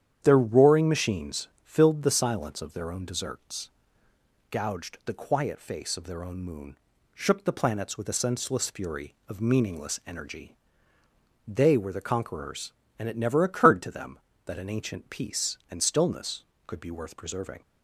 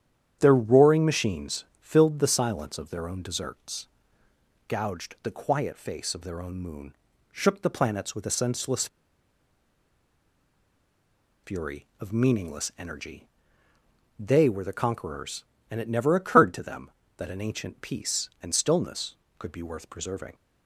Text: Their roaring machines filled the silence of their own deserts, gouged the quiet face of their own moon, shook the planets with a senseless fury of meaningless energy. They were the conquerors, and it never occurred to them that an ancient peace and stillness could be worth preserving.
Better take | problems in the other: first | starts louder than the rest; strong; until 1.4 s; 9.5 dB; strong in the first // pauses between "machines" and "filled"; slight; at 1.6 s; 0.16 s long; slight in the first // pauses between "senseless" and "fury"; strong; at 8.8 s; 2.5 s long

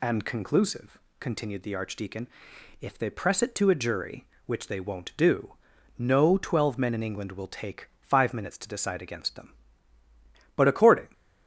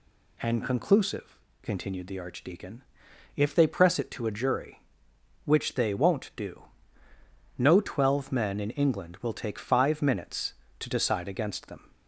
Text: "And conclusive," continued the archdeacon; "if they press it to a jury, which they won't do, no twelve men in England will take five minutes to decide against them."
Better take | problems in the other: second | goes on to say "But according"; from 10.5 s on; 0.52 s long

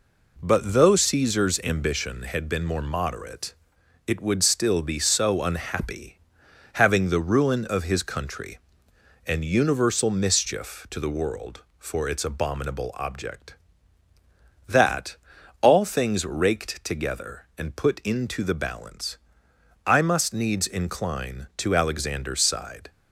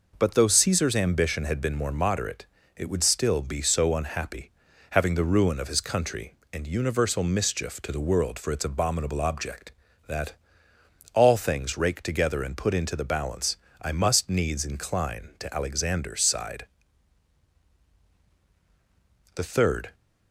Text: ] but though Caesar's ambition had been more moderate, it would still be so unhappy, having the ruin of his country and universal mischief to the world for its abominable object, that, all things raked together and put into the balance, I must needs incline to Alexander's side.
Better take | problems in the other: first | goes on to say "The third"; from 19.3 s on; 0.60 s long

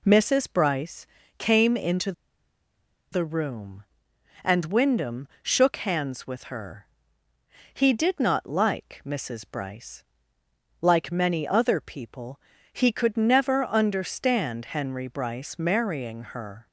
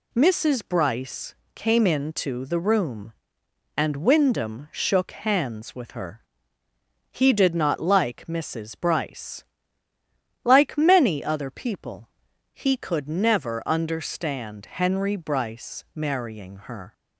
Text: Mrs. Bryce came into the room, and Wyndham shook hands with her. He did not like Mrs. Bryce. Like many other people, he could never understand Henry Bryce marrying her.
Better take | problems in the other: second | pauses between "Bryce" and "came"; slight; at 1.0 s; 0.32 s long; slight in the second // pauses between "into" and "the"; at 2.1 s; 1.0 s long

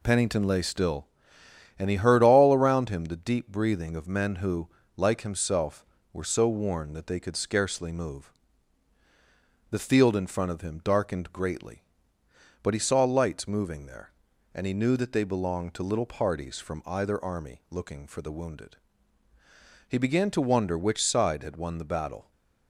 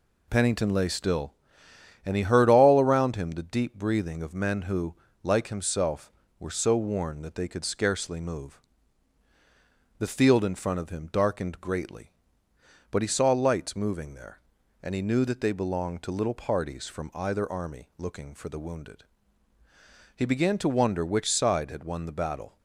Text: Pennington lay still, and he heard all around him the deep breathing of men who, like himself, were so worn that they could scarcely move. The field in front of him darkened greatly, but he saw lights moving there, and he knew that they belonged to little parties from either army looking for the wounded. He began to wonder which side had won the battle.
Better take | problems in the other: neither | none

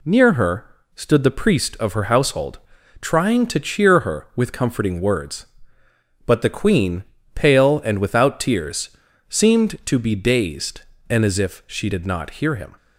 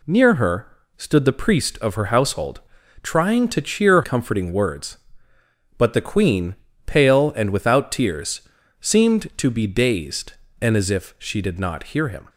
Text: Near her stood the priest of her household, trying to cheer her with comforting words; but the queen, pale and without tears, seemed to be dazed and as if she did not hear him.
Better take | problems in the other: first | pauses between "her" and "stood"; slight; at 0.6 s; 0.30 s long; slight in the first // skips "her with"; at 4.0 s

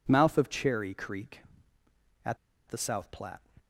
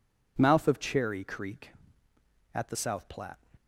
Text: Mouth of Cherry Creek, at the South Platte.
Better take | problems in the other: second | pauses between "at" and "the"; slight; at 2.3 s; 0.32 s long

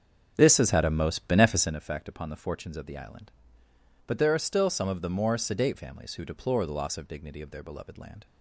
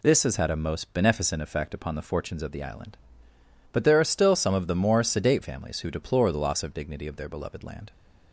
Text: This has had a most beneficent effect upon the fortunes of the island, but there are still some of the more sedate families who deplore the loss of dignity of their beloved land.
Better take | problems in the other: second | starts louder than the rest; until 1.8 s; 7 dB

